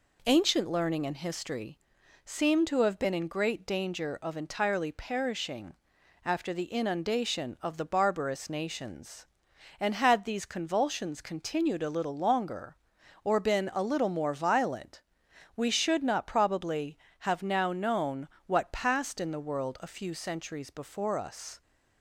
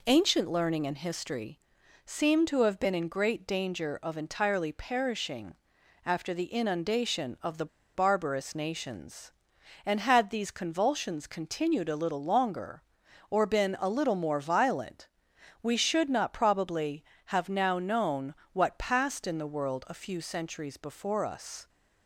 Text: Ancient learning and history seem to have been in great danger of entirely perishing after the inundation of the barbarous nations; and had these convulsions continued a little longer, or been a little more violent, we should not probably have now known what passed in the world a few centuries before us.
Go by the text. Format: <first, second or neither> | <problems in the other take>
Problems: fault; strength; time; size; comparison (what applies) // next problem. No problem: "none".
first | pauses between "history" and "seem"; noticeable; at 1.5 s; 0.48 s long; noticeable in the first // pauses between "perishing" and "after"; noticeable; at 5.5 s; 0.50 s long; noticeable in the first // pauses between "the" and "barbarous"; slight; at 7.6 s; 0.27 s long // pauses between "known" and "what"; slight; at 18.3 s; 0.18 s long; slight in the first